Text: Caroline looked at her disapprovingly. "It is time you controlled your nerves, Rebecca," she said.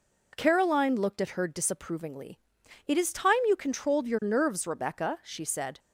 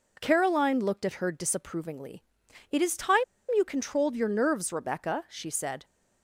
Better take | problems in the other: first | pauses between "time" and "you"; slight; at 3.2 s; 0.32 s long

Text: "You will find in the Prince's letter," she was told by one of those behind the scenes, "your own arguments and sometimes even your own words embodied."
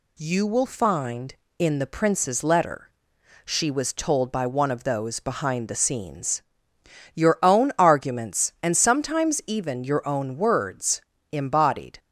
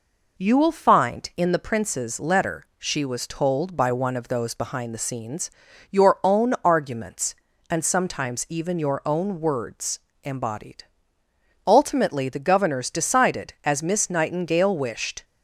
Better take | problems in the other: first | pauses between "words" and "embodied"; slight; at 9.9 s; 0.24 s long; slight in the first // goes on to say "Ultimately the Governors decided as Miss Nightingale wished"; strong; from 11.6 s on; 3.5 s long

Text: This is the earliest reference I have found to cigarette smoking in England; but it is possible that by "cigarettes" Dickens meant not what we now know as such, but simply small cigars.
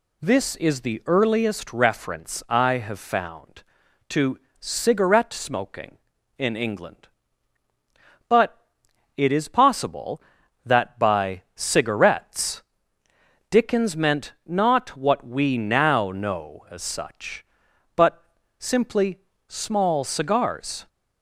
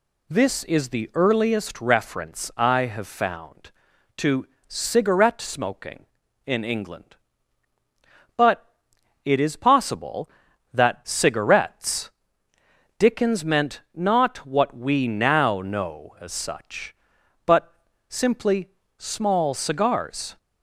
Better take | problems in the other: first | pauses between "to" and "cigarette"; slight; at 4.4 s; 0.22 s long; slight in the first // pauses between "but" and "it"; noticeable; at 8.6 s; 0.58 s long; noticeable in the first // skips "by"; at 11.0 s // pauses between "cigarettes" and "Dickens"; noticeable; at 12.1 s; 0.86 s long; noticeable in the first // pauses between "but" and "simply"; slight; at 17.7 s; 0.34 s long; slight in the first // pauses between "simply" and "small"; slight; at 18.6 s; 0.28 s long; slight in the first

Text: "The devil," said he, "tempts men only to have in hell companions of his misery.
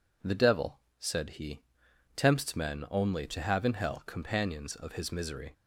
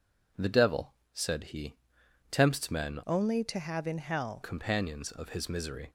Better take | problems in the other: first | changes voice from "only" to "hell"; from 3.0 to 4.4 s; 1.4 s long

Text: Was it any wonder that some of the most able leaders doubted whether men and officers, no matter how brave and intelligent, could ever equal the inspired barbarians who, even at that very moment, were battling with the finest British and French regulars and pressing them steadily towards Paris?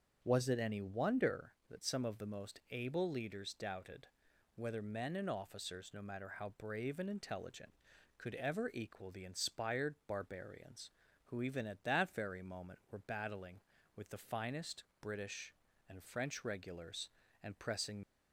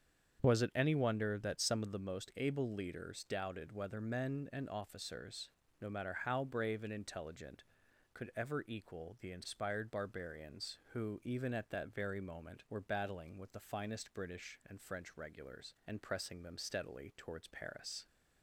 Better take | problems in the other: second | starts louder than the rest; until 1.2 s; 6.5 dB; strong in the second // pauses between "doubted" and "whether"; noticeable; at 4.0 s; 0.48 s long // pauses between "finest" and "British"; slight; at 14.8 s; 0.18 s long // stops before "them steadily towards Paris"; at 18.0 s

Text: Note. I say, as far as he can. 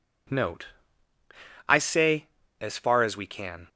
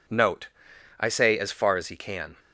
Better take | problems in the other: second | says "we" for "he"; at 3.1 s

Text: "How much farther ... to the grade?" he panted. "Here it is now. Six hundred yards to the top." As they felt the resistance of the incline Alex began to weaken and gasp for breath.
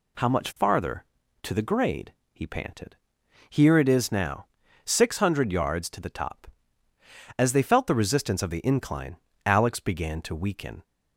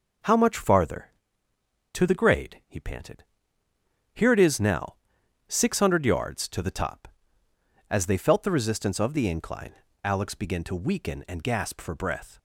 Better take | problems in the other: second | pauses between "incline" and "Alex"; slight; at 9.1 s; 0.30 s long; slight in the second // stops before "and gasp for breath"; at 10.8 s

